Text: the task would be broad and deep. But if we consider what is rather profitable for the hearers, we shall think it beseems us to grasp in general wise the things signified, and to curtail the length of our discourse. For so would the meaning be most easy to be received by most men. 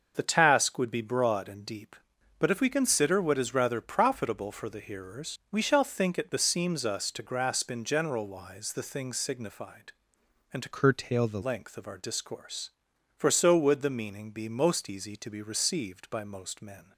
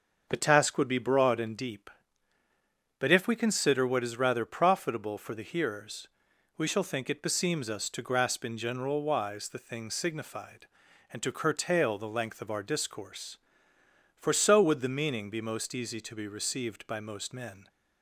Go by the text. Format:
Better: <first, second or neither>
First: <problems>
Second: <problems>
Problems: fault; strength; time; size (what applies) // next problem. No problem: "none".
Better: second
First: starts louder than the rest; until 1.1 s; 6.5 dB // changes voice from "curtail" to "the"; from 10.7 to 11.4 s; 0.7 s long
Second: starts louder than the rest; until 1.3 s; 6.5 dB